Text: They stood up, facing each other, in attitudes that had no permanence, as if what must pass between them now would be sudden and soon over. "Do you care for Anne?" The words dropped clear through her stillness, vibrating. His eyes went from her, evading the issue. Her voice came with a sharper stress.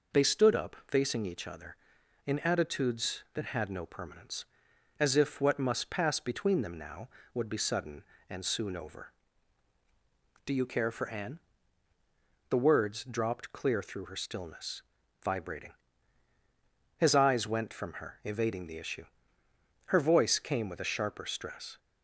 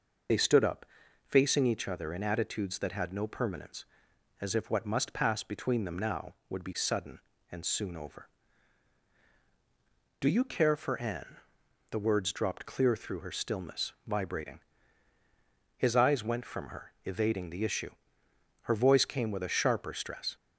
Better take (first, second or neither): first